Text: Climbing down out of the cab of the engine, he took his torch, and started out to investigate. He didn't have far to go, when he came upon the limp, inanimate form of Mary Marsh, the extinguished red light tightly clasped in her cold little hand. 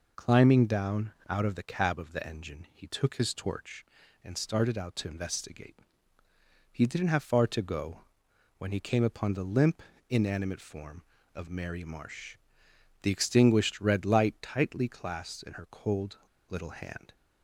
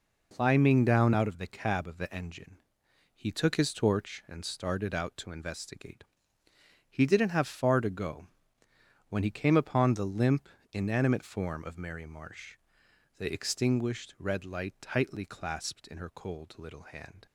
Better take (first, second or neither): second